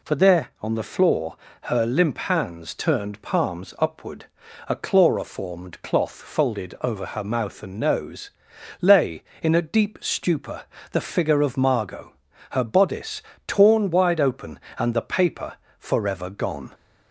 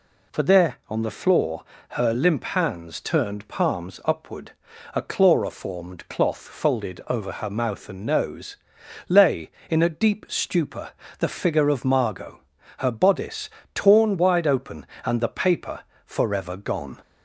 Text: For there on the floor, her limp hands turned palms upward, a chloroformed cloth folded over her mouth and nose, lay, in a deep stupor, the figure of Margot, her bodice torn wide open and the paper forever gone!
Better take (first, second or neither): neither